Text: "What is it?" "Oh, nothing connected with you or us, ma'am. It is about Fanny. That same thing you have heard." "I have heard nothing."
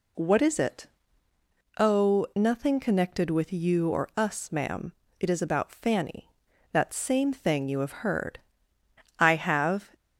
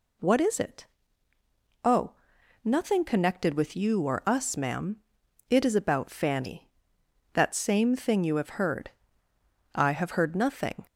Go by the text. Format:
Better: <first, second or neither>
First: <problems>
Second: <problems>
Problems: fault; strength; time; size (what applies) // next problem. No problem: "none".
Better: second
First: stops before "heard nothing"; at 9.9 s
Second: none